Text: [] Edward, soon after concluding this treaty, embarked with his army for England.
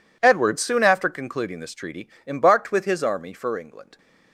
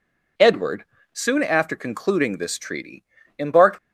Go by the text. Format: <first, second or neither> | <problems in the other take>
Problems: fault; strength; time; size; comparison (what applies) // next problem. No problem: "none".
first | stops before "with his army for England"; at 3.7 s